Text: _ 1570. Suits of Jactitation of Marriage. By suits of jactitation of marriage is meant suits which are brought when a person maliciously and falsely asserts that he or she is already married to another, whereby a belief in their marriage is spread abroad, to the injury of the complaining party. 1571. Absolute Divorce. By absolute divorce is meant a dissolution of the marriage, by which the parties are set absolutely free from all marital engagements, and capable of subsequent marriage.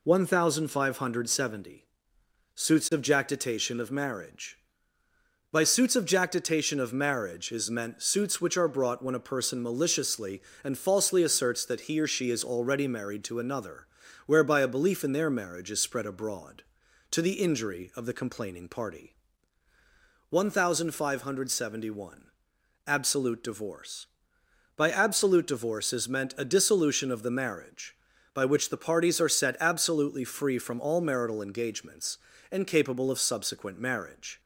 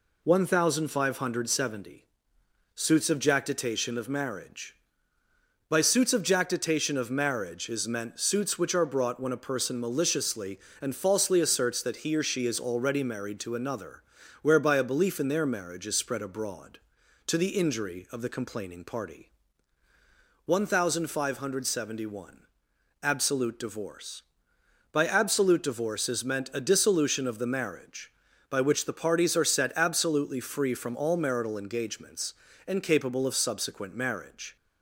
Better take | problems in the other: neither | none

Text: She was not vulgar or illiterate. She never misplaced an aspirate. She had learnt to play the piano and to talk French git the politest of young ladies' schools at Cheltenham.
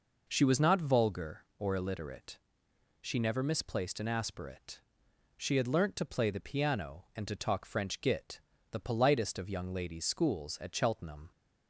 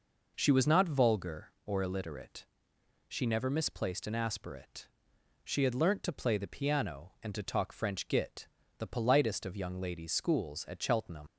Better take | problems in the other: first | pauses between "git" and "the"; slight; at 8.4 s; 0.30 s long; slight in the first // leaves "Cheltenham" unfinished; at 11.2 s; 110 ms

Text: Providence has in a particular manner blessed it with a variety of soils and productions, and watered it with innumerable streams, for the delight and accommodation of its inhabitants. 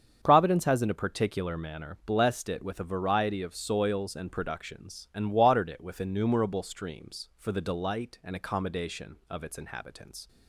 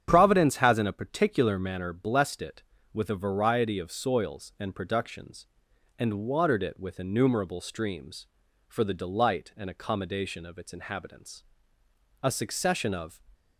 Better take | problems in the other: first | starts louder than the rest; strong; until 1.1 s; 8.5 dB; strong in the first // goes on to say "A succession of"; noticeable; from 12.2 s on; 0.98 s long

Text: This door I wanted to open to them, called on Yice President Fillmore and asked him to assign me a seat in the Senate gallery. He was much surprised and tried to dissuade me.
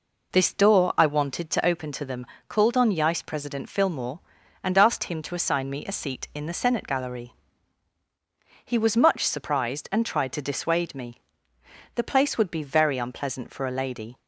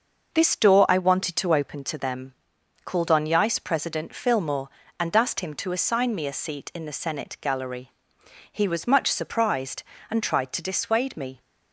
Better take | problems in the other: second | goes on to say "The place would be very unpleasant for a lady"; strong; from 11.9 s on; 2.2 s long

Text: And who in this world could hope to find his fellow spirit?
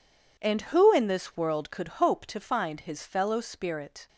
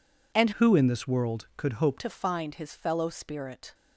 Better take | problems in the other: first | changes voice from "who" to "hope"; from 0.5 to 1.9 s; 1.4 s long

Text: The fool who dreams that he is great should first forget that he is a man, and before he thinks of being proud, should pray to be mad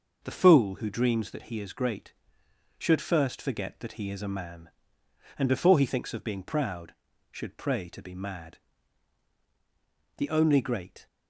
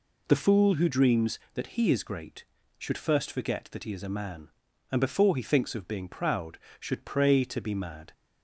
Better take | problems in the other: second | goes on to say "The only great"; noticeable; from 10.1 s on; 0.88 s long

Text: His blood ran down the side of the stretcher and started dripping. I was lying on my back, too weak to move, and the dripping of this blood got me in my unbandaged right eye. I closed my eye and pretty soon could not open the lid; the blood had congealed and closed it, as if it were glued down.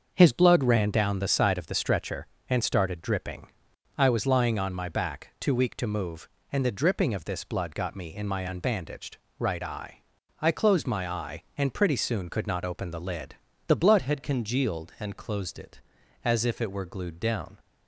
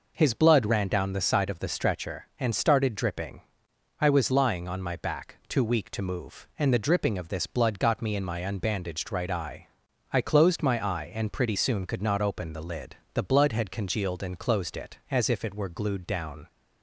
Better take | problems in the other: second | starts louder than the rest; until 1.1 s; 6.5 dB // pauses between "unbandaged" and "right"; slight; at 9.1 s; 0.22 s long // changes voice at "had"; from 14.0 s on; 3.5 s long

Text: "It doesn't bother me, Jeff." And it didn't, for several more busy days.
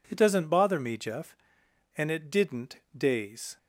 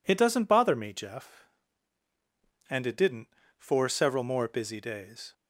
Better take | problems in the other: second | skips "for several more busy"; at 2.8 s

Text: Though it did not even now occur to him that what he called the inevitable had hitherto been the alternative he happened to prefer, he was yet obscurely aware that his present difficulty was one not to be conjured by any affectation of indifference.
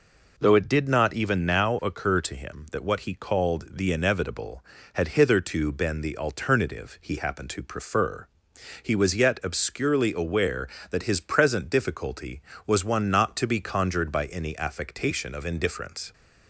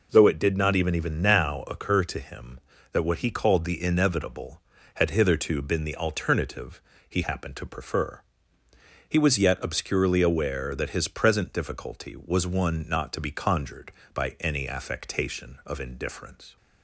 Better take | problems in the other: first | says "even" twice; at 0.9 s // pauses between "alternative" and "he"; slight; at 6.8 s; 0.26 s long

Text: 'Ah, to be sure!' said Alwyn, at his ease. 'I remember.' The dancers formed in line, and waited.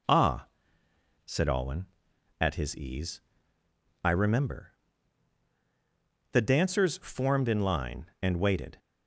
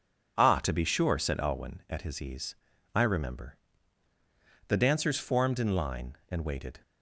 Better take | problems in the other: second | skips "to be sure"; at 0.8 s

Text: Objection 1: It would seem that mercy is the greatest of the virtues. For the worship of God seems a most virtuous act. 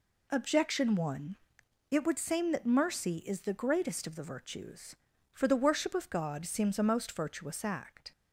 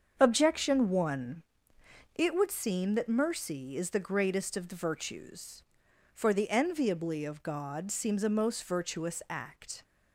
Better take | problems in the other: first | starts louder than the rest; until 1.1 s; 7 dB // says "enviably" for "worship"; at 6.4 s

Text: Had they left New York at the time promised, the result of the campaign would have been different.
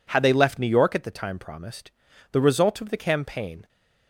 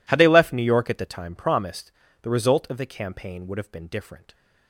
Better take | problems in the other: second | stops before "would have been different"; at 3.6 s

